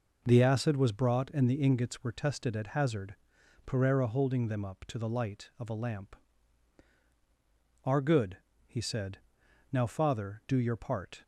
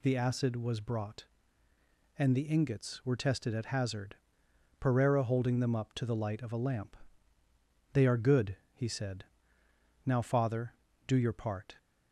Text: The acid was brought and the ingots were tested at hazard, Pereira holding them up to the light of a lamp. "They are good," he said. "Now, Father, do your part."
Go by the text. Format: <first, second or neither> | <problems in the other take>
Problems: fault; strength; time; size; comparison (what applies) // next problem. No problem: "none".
second | skips "They"; at 6.9 s